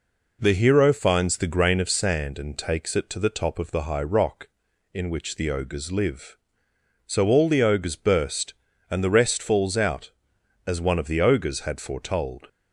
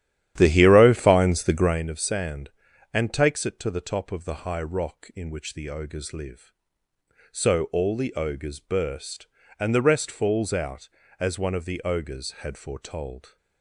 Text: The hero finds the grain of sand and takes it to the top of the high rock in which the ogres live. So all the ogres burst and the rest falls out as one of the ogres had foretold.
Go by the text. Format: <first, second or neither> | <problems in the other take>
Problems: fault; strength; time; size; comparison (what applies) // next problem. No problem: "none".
first | starts louder than the rest; strong; until 1.9 s; 11.5 dB